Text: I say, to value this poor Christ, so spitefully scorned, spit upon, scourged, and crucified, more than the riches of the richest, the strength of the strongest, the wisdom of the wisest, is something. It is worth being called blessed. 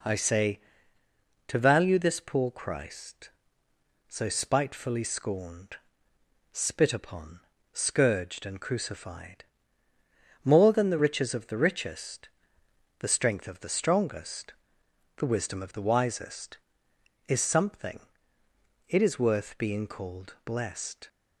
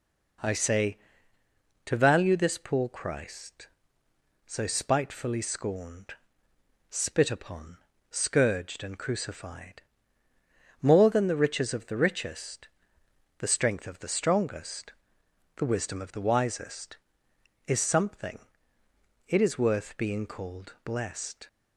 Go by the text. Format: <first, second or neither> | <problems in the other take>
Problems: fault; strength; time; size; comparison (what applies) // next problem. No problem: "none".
neither | none